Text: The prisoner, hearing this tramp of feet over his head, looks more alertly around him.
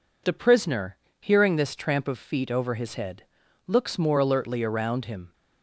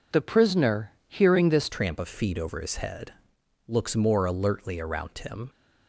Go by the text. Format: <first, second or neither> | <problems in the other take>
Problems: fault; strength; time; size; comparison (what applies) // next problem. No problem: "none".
first | changes voice at "tramp"; from 1.6 s on; 3.8 s long